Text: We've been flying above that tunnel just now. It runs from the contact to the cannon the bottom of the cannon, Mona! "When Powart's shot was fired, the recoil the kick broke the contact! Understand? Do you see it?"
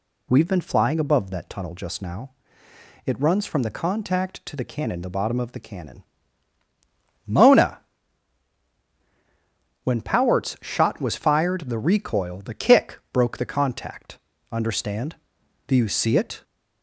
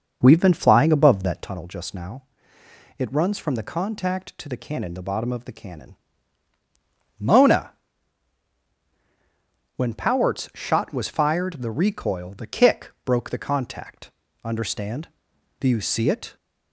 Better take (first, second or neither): first